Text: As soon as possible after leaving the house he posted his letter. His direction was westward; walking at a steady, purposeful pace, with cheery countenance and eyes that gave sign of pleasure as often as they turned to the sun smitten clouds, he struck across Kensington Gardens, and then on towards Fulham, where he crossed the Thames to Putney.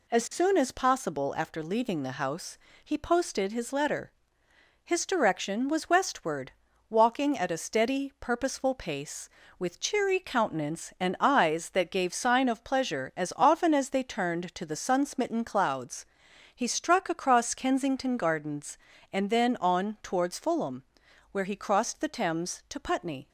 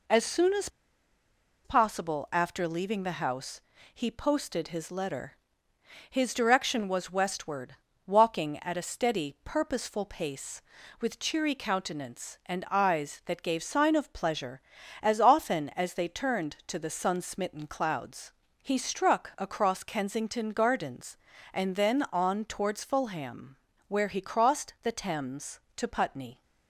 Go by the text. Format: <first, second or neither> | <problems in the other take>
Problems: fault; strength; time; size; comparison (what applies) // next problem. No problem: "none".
first | pauses between "as" and "possible"; noticeable; at 0.6 s; 0.96 s long // pauses between "house" and "he"; slight; at 3.6 s; 0.32 s long; slight in the first